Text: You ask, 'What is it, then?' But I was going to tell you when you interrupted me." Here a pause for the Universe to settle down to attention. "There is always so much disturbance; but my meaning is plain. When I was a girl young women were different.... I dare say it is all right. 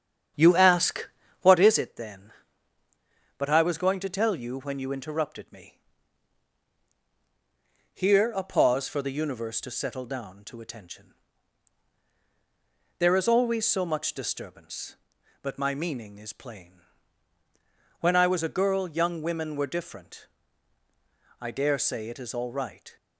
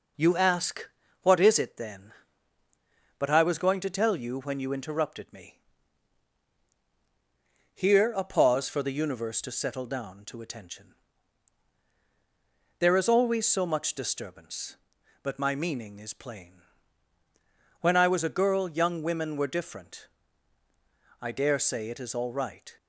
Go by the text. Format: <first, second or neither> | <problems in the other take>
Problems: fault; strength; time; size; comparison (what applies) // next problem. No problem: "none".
second | starts louder than the rest; strong; until 1.7 s; 8.5 dB